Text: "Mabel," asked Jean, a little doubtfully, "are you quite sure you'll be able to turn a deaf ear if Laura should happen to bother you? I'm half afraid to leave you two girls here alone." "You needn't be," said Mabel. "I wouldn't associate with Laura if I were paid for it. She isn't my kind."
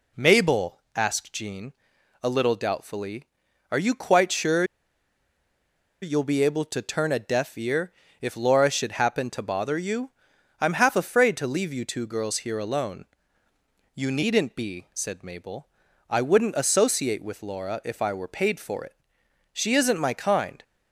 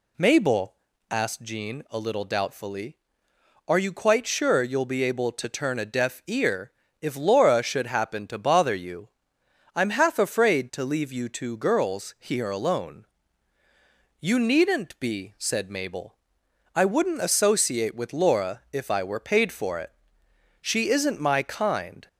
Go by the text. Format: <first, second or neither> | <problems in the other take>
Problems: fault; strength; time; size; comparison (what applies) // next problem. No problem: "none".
second | pauses between "sure" and "you'll"; strong; at 4.6 s; 1.3 s long // pauses between "ear" and "if"; slight; at 7.9 s; 0.30 s long; slight in the second